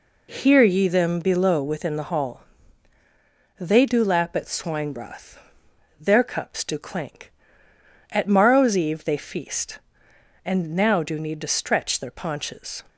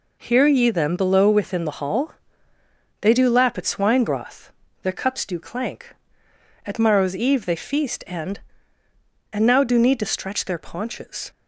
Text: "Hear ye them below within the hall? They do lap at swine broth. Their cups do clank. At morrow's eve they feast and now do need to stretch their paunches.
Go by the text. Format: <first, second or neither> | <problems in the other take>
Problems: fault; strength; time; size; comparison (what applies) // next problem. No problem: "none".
first | says "and" twice; at 9.3 s